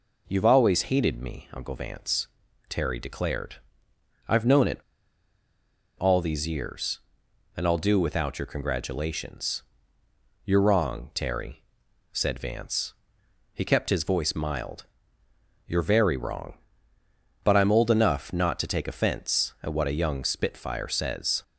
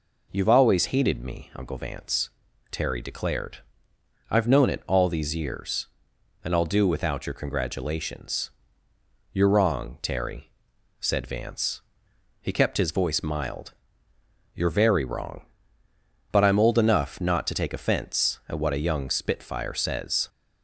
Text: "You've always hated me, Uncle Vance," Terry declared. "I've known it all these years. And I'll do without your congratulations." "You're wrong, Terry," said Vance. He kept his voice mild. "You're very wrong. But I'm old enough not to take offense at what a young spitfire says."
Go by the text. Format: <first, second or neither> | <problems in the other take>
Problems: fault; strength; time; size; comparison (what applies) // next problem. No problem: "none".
second | pauses between "it" and "all"; at 4.7 s; 1.1 s long